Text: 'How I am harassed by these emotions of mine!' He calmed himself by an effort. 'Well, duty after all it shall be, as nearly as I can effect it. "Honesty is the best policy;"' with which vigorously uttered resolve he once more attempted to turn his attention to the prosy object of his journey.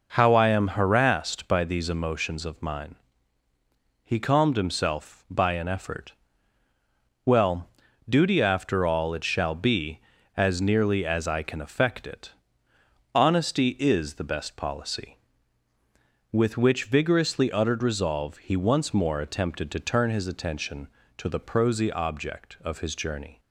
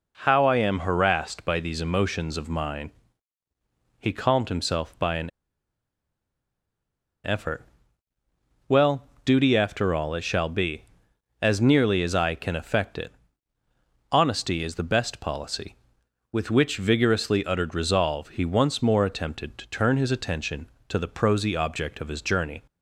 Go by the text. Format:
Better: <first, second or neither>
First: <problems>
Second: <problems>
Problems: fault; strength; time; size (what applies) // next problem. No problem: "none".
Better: first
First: none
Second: pauses between "an" and "effort"; strong; at 5.2 s; 1.9 s long